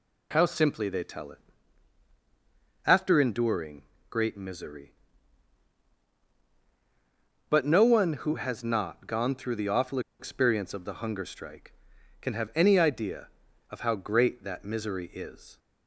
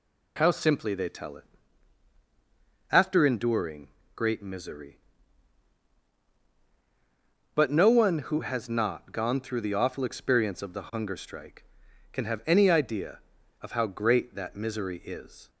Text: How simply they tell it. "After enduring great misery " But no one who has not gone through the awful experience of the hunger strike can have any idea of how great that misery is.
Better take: second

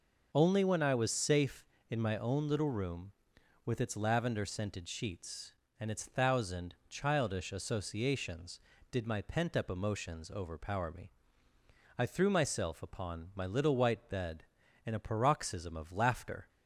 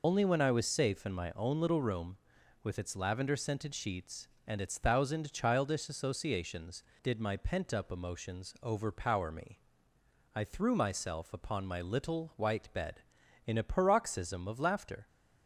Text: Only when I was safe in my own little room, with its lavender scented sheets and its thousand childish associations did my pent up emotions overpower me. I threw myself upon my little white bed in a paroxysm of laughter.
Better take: first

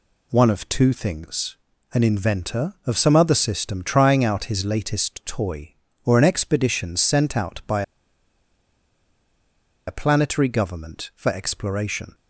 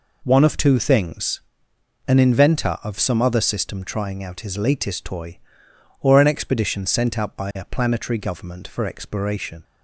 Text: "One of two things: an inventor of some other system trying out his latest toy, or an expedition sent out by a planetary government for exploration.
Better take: second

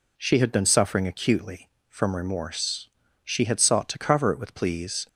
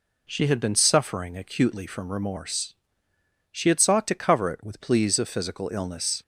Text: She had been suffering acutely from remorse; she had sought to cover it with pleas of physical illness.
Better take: second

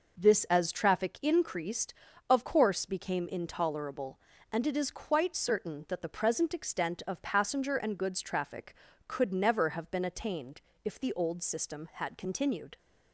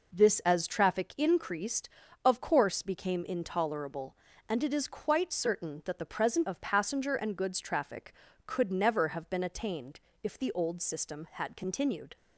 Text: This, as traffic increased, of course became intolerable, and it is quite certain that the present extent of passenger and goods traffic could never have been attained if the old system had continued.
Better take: first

